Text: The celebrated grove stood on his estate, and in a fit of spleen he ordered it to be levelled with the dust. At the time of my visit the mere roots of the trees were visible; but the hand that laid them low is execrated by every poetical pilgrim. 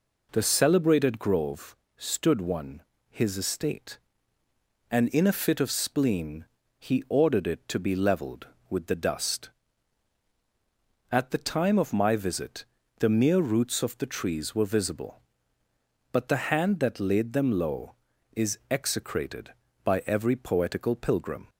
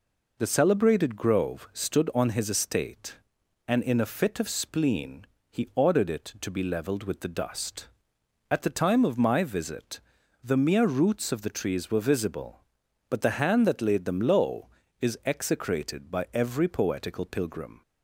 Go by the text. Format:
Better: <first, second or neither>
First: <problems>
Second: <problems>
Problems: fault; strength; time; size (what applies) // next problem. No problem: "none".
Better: second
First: pauses between "grove" and "stood"; slight; at 1.7 s; 0.22 s long // says "one" for "on"; at 2.3 s // pauses between "spleen" and "he"; slight; at 6.4 s; 0.32 s long // pauses between "visit" and "the"; slight; at 12.6 s; 0.34 s long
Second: pauses between "spleen" and "he"; slight; at 5.2 s; 0.24 s long // pauses between "visit" and "the"; at 9.9 s; 0.44 s long